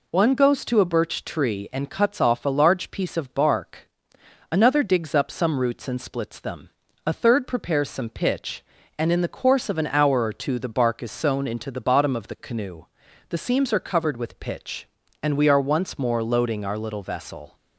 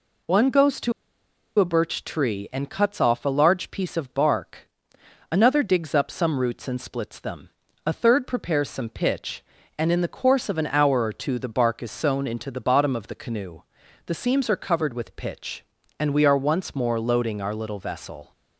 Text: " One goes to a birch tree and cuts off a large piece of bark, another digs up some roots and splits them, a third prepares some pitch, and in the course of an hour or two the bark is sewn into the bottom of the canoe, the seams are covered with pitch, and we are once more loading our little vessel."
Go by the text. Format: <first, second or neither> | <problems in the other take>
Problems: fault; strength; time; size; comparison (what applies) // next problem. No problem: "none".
first | pauses between "to" and "a"; noticeable; at 0.9 s; 0.67 s long